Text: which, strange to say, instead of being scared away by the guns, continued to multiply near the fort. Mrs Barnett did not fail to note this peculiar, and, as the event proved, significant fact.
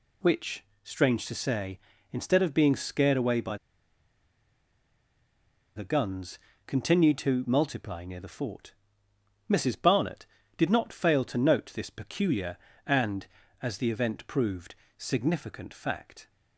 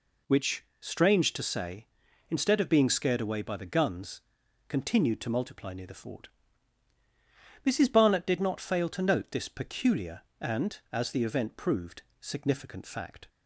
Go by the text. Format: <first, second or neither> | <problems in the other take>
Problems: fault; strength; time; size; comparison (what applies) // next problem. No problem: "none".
second | pauses between "by" and "the"; strong; at 3.5 s; 2.2 s long